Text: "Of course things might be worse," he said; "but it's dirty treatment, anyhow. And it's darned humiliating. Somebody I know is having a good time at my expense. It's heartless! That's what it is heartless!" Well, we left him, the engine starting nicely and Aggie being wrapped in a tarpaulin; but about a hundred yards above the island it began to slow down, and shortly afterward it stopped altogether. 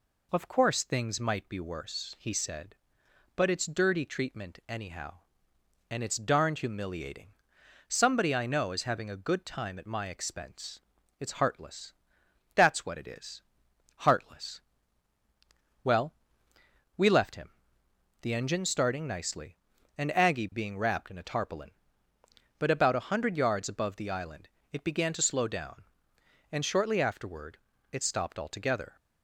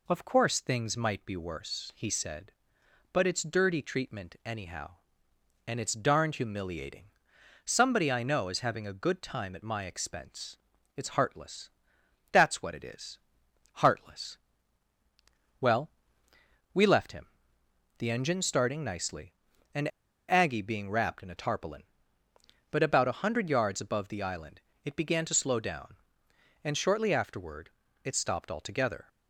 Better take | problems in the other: first | pauses between "is" and "heartless"; noticeable; at 13.1 s; 0.64 s long; noticeable in the first // pauses between "and" and "Aggie"; at 19.9 s; 0.39 s long // pauses between "island" and "it"; slight; at 24.5 s; 0.24 s long; slight in the first // pauses between "afterward" and "it"; slight; at 27.6 s; 0.34 s long; slight in the first

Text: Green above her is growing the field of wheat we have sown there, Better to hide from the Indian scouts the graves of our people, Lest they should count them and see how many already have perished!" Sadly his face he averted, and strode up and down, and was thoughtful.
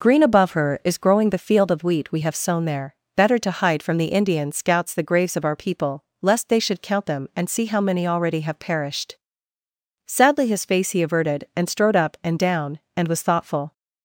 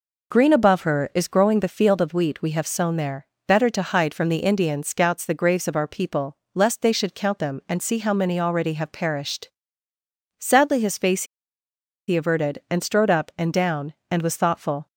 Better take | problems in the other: first | pauses between "face" and "he"; noticeable; at 11.2 s; 0.84 s long

